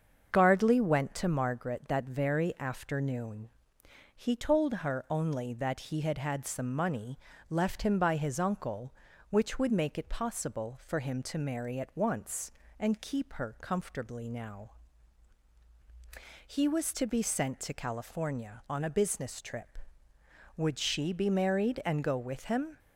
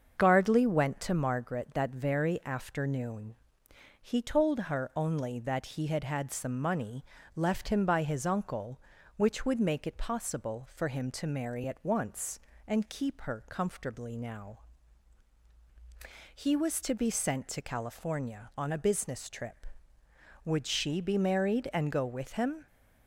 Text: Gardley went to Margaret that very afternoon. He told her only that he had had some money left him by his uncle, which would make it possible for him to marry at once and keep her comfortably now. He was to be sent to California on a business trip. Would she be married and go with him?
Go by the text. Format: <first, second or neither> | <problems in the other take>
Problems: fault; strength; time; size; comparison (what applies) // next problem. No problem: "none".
neither | starts louder than the rest; the same in both // pauses between "money" and "left"; slight; the same in both